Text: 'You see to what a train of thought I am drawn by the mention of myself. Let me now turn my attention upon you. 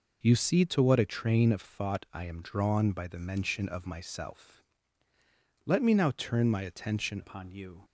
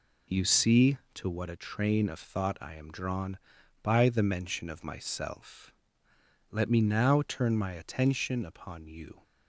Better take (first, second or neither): second